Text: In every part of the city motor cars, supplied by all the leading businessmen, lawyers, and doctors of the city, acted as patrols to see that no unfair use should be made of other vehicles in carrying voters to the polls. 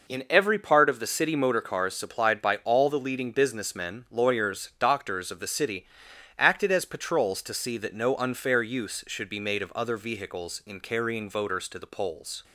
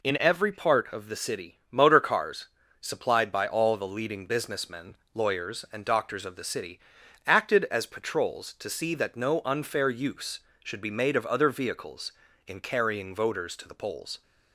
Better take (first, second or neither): second